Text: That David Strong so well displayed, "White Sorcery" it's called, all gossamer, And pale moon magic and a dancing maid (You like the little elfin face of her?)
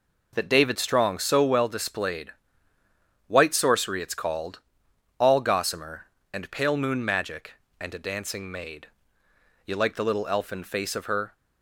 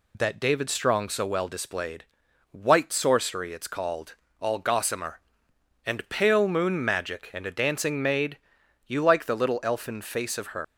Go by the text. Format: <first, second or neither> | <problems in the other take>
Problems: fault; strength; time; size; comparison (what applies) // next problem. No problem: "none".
first | leaves "her" unfinished; at 10.6 s; 130 ms